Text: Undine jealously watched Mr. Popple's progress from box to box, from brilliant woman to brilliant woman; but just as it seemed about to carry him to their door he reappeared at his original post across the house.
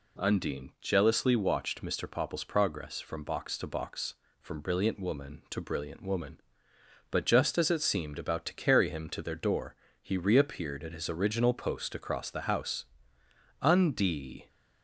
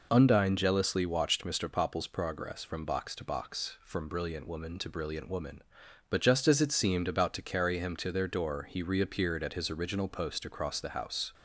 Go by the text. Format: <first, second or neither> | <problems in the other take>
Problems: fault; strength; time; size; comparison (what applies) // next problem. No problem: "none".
second | pauses between "door" and "he"; slight; at 9.7 s; 0.26 s long // goes on to say "Undie"; noticeable; from 13.6 s on; 0.86 s long